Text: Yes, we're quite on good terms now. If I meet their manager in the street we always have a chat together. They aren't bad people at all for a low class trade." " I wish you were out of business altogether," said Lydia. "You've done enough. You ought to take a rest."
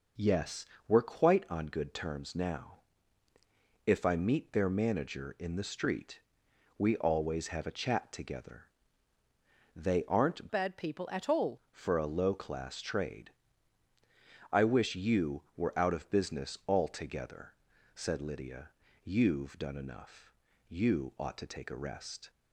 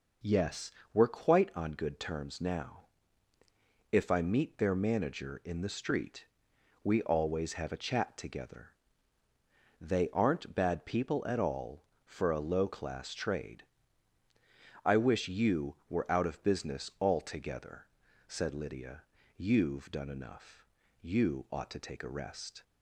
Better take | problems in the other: second | pauses between "street" and "we"; noticeable; at 6.2 s; 0.58 s long; noticeable in the second // changes voice from "bad" to "all"; from 10.5 to 11.5 s; 1.0 s long

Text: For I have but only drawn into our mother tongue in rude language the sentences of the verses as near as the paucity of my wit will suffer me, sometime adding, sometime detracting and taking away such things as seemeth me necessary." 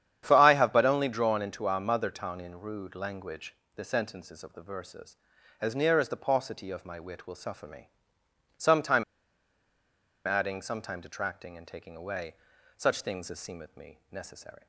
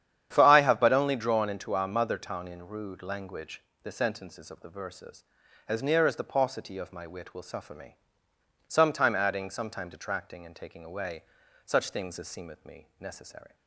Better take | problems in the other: second | starts louder than the rest; strong; until 1.2 s; 9.5 dB; strong in the second // pauses between "language" and "the"; slight; at 3.5 s; 0.20 s long; slight in the second // pauses between "sometime" and "adding"; at 9.0 s; 1.2 s long // pauses between "away" and "such"; at 12.3 s; 0.42 s long; also in the second

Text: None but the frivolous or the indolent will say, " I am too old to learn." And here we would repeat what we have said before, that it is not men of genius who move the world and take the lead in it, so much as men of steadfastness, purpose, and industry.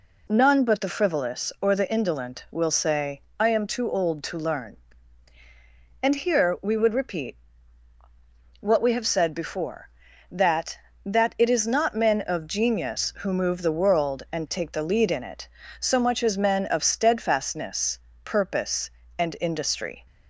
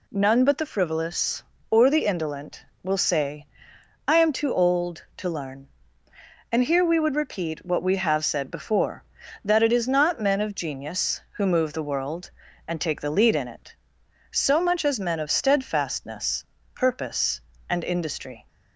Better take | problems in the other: second | pauses between "repeat" and "what"; strong; at 7.3 s; 1.2 s long // says "that" twice; at 11.0 s

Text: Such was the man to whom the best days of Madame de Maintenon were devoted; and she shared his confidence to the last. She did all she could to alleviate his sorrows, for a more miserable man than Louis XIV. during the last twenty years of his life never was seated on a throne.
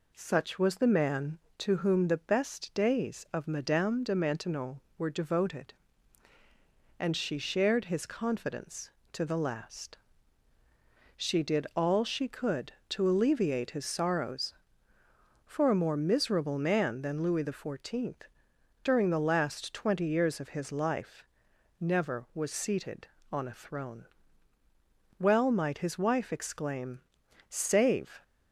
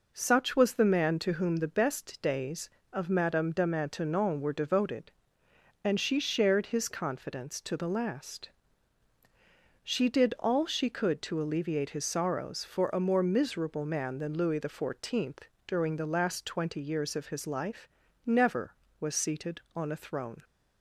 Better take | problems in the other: second | pauses between "life" and "never"; noticeable; at 21.2 s; 0.56 s long; also in the second // goes on to say "Well might his wife exclaim Save"; strong; from 25.1 s on; 3.0 s long

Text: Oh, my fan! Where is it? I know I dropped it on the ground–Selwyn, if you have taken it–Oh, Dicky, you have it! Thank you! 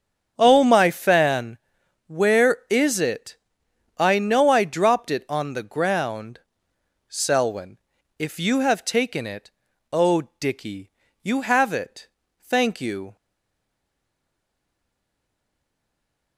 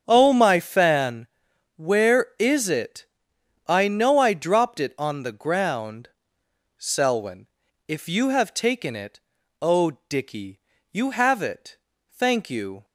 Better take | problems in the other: second | starts louder than the rest; strong; until 1.3 s; 7.5 dB; strong in the second // stays silent after the last word; strong; from 13.1 s on; 3.2 s long

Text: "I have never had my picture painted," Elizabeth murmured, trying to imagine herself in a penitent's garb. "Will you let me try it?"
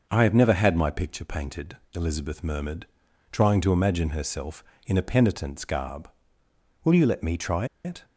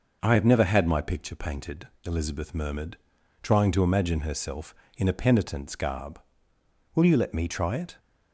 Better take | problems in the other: second | pauses between "try" and "it"; slight; at 7.6 s; 0.18 s long

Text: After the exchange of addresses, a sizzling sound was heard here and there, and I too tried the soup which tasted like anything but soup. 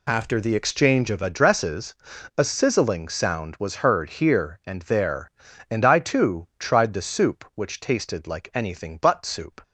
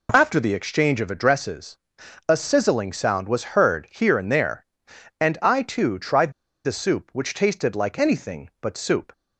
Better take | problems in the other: first | pauses between "tried" and "the"; slight; at 6.3 s; 0.32 s long

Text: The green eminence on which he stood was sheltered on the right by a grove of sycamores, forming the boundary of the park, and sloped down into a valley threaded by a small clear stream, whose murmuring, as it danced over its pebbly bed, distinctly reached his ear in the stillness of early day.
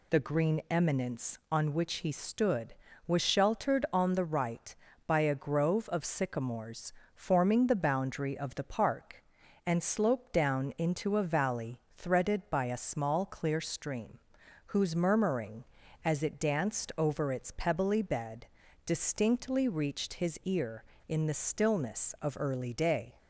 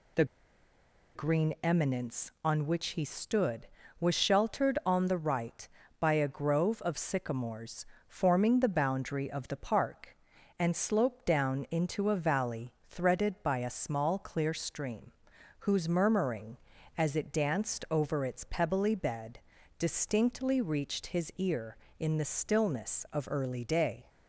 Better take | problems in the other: first | pauses between "The" and "green"; noticeable; at 0.2 s; 0.90 s long // pauses between "valley" and "threaded"; slight; at 12.7 s; 0.16 s long; slight in the first

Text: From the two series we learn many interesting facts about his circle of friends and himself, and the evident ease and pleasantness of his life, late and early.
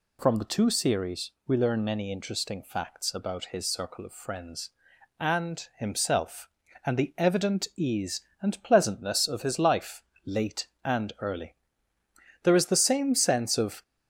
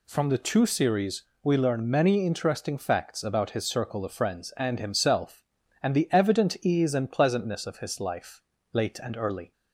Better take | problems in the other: second | pauses between "series" and "we"; slight; at 1.3 s; 0.16 s long; slight in the second // goes on to say "There is the same sense of"; from 12.4 s on; 1.4 s long

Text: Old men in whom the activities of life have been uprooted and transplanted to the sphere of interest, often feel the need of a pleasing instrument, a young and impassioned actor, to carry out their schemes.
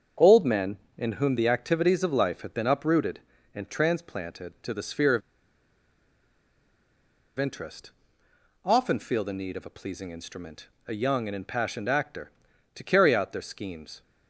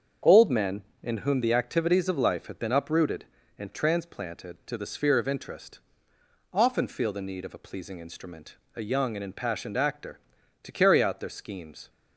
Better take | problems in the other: second | starts louder than the rest; until 1.3 s; 7 dB; also in the second // pauses between "of" and "interest"; strong; at 5.2 s; 2.1 s long

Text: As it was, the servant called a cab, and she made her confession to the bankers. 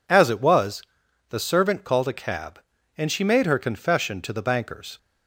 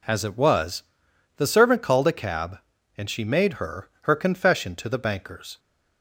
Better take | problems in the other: first | says "her" twice; at 4.0 s

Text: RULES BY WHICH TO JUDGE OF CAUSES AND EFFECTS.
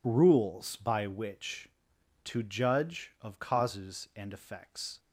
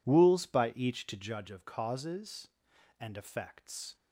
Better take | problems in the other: first | says "Each" for "WHICH"; at 0.7 s

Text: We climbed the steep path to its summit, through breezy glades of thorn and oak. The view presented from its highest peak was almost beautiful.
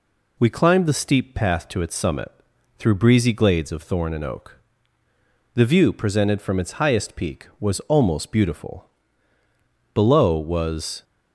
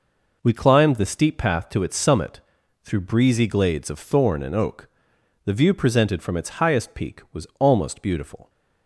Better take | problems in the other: second | goes on to say "Below was"; noticeable; from 9.9 s on; 1.1 s long

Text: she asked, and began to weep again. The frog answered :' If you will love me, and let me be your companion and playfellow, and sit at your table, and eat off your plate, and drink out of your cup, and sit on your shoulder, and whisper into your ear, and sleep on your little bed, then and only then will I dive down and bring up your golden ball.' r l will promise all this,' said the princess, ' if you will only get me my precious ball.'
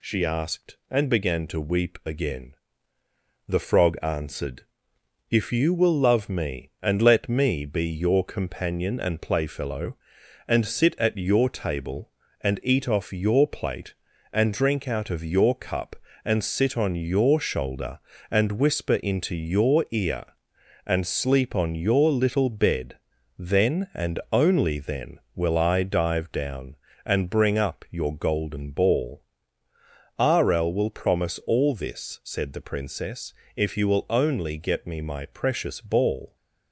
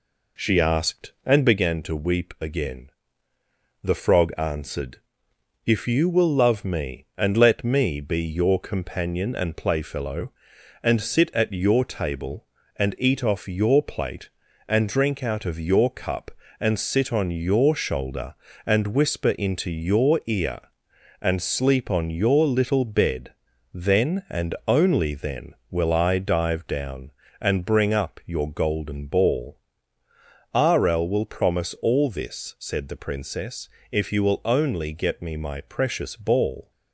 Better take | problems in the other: first | starts louder than the rest; until 1.8 s; 3.5 dB

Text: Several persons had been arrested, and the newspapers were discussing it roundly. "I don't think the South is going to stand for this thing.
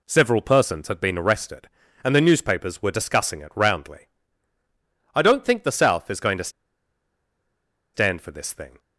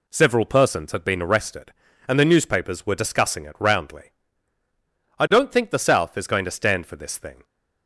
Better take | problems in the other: second | pauses between "to" and "stand"; strong; at 6.4 s; 1.4 s long

